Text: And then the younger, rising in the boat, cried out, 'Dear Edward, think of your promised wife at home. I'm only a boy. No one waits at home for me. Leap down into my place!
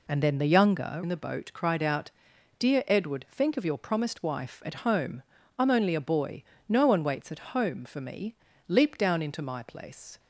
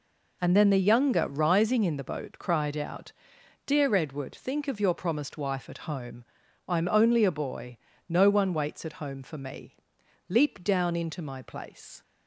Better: second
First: skips "rising"; at 1.0 s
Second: none

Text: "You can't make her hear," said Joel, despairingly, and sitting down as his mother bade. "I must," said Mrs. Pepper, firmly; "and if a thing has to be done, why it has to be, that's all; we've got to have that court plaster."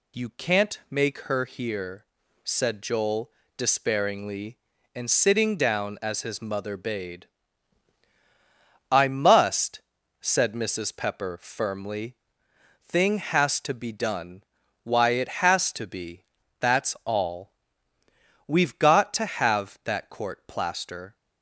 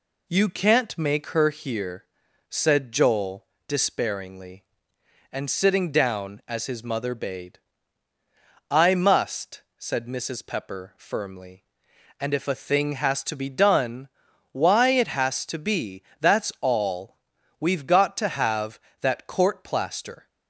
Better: second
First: skips "and if a"; at 12.4 s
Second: none

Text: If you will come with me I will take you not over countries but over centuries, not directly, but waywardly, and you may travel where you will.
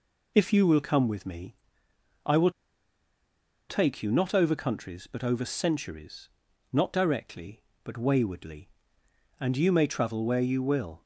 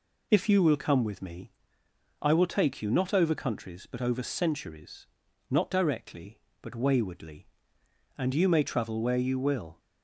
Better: second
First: pauses between "me" and "I"; noticeable; at 1.5 s; 0.70 s long // pauses between "will" and "take"; at 2.5 s; 1.1 s long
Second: pauses between "me" and "I"; noticeable; at 1.5 s; 0.70 s long

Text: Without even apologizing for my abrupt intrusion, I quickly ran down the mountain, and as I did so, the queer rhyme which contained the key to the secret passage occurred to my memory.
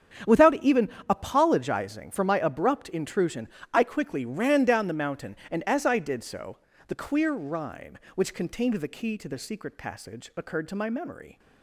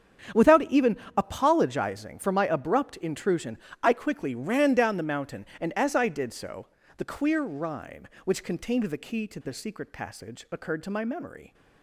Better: neither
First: starts louder than the rest; strong; until 1.4 s; 8.5 dB // pauses between "even" and "apologizing"; slight; at 0.8 s; 0.20 s long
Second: starts louder than the rest; strong; until 1.5 s; 8 dB // pauses between "even" and "apologizing"; slight; at 0.9 s; 0.20 s long

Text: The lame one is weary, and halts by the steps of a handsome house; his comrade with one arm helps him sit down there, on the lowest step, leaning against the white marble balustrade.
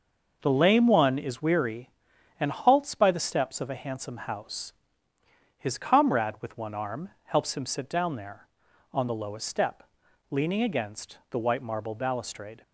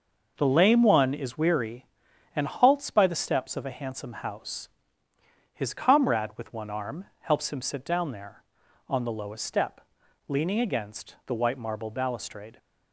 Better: neither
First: none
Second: none

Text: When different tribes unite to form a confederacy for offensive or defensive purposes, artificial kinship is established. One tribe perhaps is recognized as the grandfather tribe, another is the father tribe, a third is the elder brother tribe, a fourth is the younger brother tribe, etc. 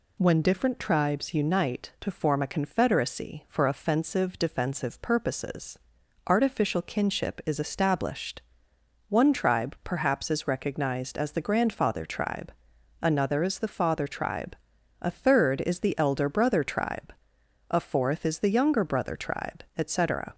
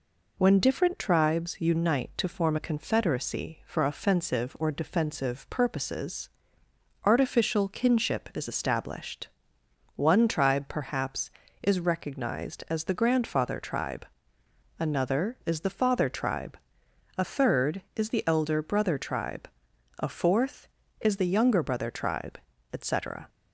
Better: second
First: skips "or"; at 4.3 s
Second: none

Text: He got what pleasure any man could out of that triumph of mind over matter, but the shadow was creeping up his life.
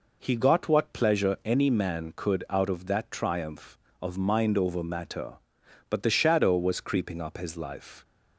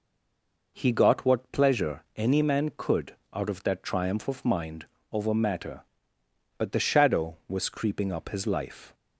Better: first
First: none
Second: stays silent before the first word; slight; until 0.7 s; 0.7 s long // pauses between "could" and "out"; slight; at 3.1 s; 0.18 s long // pauses between "mind" and "over"; slight; at 4.8 s; 0.26 s long

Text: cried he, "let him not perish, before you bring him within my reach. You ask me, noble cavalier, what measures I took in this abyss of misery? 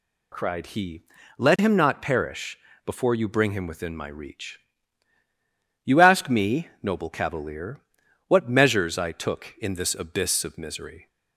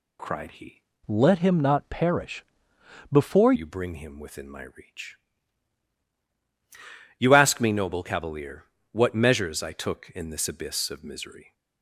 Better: first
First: none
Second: changes voice from "let" to "before"; from 1.0 to 3.5 s; 2.5 s long

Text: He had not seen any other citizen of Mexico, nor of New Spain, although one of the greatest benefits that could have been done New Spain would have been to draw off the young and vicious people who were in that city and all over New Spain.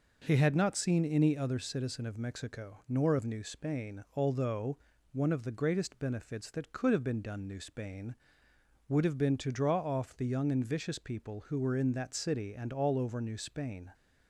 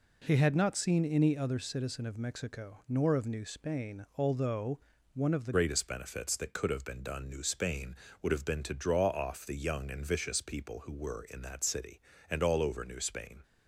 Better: first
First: pauses between "although" and "one"; slight; at 4.7 s; 0.36 s long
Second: pauses between "although" and "one"; slight; at 4.7 s; 0.36 s long // changes voice at "greatest"; from 5.5 s on; 7.9 s long

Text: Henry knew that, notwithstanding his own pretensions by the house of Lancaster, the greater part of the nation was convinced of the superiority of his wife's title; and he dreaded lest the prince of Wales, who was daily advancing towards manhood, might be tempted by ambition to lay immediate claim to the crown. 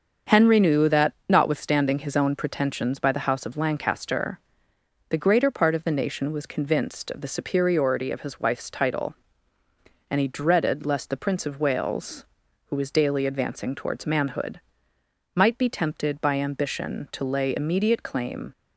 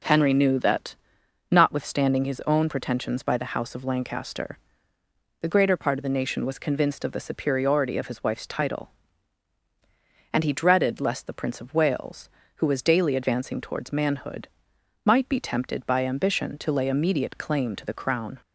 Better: second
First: starts louder than the rest; until 1.4 s; 7 dB // stops before "to the crown"; at 18.5 s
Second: none

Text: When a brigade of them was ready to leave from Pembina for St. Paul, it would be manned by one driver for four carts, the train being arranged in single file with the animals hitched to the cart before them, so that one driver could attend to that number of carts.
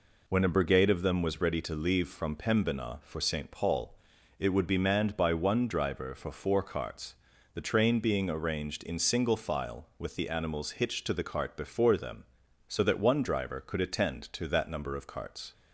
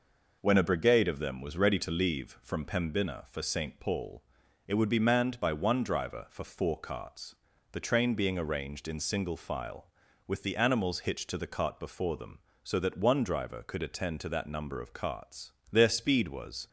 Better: first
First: none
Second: goes on to say "Their speed was"; noticeable; from 15.7 s on; 0.96 s long

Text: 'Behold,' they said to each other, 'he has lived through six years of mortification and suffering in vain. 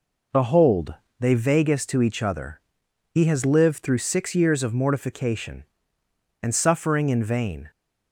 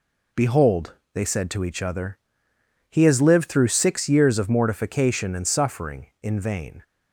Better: second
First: says "vagus" for "said"; at 1.3 s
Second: none

